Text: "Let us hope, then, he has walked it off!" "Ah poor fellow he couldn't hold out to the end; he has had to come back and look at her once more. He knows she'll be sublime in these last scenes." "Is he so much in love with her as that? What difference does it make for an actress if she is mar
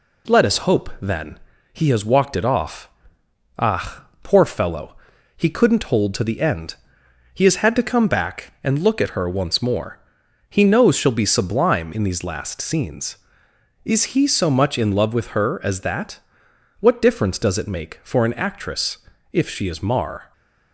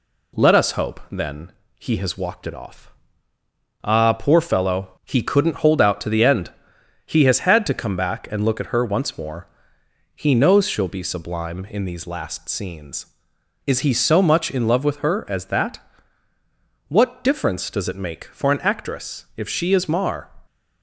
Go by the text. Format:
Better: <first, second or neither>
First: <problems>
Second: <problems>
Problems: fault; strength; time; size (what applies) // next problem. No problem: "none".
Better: second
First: pauses between "Ah" and "poor"; slight; at 4.0 s; 0.20 s long // pauses between "fellow" and "he"; at 4.9 s; 0.40 s long // skips "out"; at 6.1 s // pauses between "actress" and "if"; slight; at 18.9 s; 0.34 s long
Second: none